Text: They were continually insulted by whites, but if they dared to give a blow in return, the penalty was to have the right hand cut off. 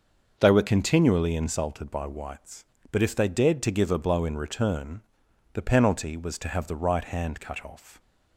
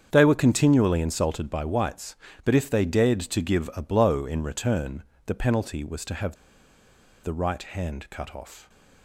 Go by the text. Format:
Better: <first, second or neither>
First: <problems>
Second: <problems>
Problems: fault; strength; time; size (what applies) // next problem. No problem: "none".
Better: first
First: starts louder than the rest; noticeable; until 1.4 s; 6 dB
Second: starts louder than the rest; strong; until 1.1 s; 7.5 dB // pauses between "have" and "the"; noticeable; at 6.3 s; 0.86 s long